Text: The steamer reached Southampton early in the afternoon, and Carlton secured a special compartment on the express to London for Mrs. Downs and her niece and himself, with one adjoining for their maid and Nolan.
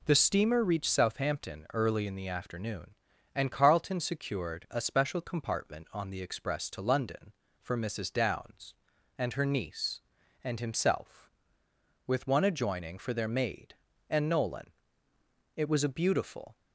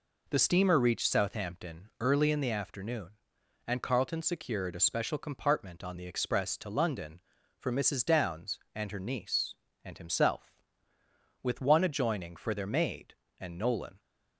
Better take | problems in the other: second | goes on to say "It was a beautiful"; noticeable; from 15.5 s on; 1.0 s long

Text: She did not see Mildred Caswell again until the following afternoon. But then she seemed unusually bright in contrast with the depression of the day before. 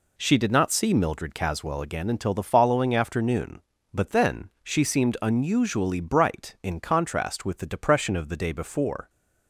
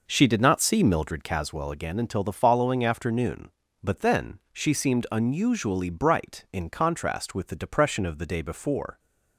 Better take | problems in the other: first | starts louder than the rest; noticeable; until 1.3 s; 5.5 dB

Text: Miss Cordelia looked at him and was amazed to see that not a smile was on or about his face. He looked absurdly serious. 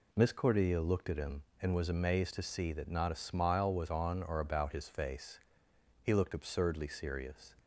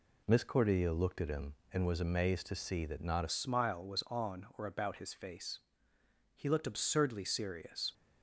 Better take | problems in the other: first | changes voice at "smile"; from 3.2 s on; 4.7 s long

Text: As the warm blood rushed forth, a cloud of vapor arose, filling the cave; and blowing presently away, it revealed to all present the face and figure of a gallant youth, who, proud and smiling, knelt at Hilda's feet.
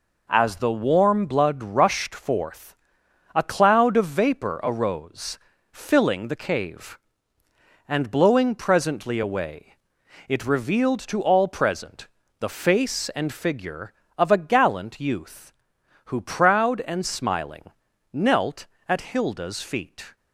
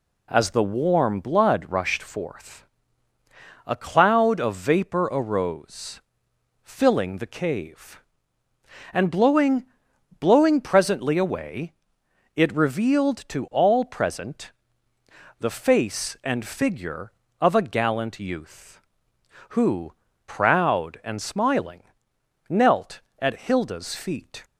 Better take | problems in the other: first | says "blowing" twice; at 10.1 s // pauses between "present" and "the"; noticeable; at 14.5 s; 0.86 s long; slight in the first

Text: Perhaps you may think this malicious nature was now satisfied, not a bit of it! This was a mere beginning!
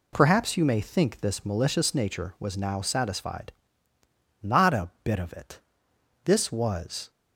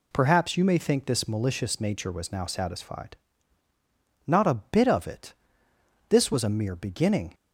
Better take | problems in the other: second | stops before "a mere beginning"; at 7.0 s

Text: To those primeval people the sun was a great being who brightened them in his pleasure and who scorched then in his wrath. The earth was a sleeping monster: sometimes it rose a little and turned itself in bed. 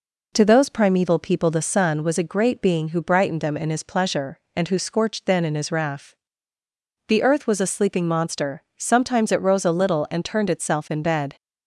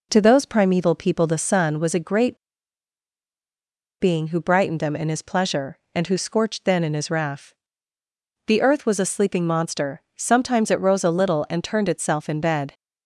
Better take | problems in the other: first | pauses between "great" and "being"; strong; at 2.3 s; 1.6 s long

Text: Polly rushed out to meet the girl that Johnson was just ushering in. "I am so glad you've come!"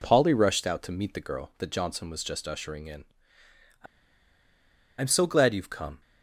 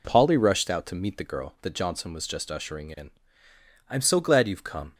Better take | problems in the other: second | pauses between "I" and "am"; at 3.8 s; 1.1 s long

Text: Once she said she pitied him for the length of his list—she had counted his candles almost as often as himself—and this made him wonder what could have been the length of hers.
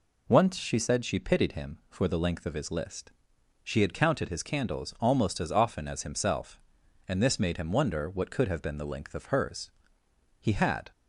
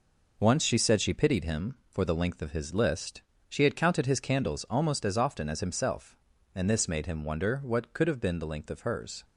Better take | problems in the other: second | goes on to say "He had"; from 10.4 s on; 0.50 s long

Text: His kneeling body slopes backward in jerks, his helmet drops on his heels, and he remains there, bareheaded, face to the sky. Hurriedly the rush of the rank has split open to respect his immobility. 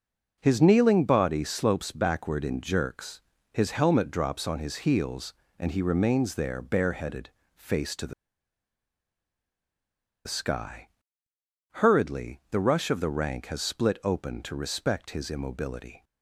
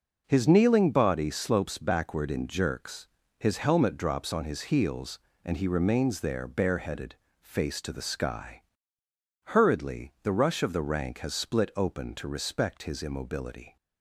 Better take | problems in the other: second | pauses between "the" and "sky"; strong; at 8.1 s; 2.1 s long

